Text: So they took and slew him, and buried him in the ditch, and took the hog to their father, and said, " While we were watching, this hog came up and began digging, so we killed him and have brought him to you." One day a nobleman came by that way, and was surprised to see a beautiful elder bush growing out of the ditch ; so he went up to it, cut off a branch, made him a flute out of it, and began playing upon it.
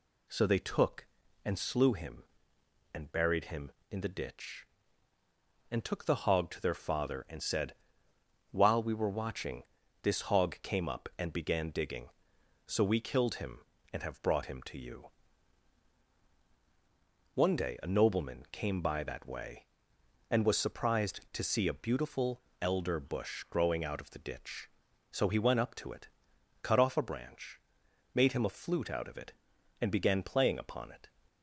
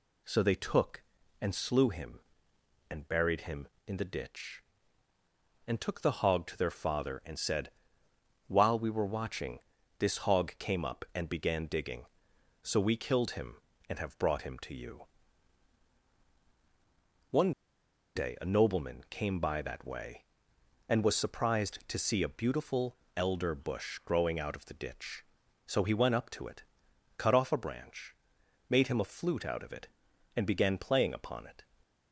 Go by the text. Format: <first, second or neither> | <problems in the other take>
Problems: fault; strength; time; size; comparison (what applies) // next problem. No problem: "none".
first | pauses between "One" and "day"; noticeable; at 17.5 s; 0.64 s long // pauses between "beautiful" and "elder"; slight; at 22.9 s; 0.20 s long; slight in the first